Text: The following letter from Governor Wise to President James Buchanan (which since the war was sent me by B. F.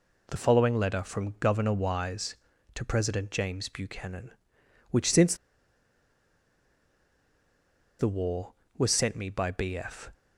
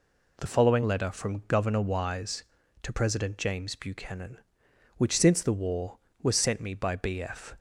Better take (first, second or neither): second